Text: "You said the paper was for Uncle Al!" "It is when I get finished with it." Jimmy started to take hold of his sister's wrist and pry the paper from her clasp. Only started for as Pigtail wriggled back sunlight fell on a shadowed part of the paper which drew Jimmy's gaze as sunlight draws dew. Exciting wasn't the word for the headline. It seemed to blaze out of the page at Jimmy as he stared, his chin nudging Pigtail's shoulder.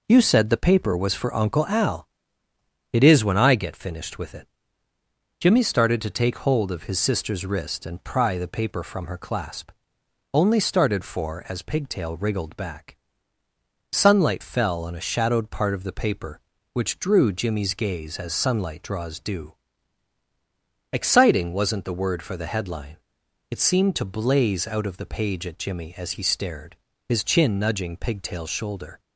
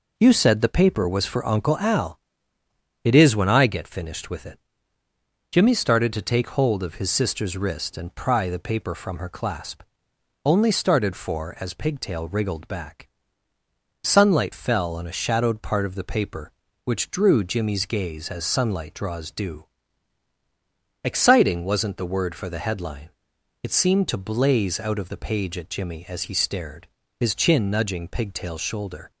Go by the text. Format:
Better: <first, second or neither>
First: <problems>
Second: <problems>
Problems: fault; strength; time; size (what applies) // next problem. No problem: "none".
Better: neither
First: pauses between "back" and "sunlight"; noticeable; at 12.9 s; 0.94 s long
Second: pauses between "back" and "sunlight"; noticeable; at 13.0 s; 0.94 s long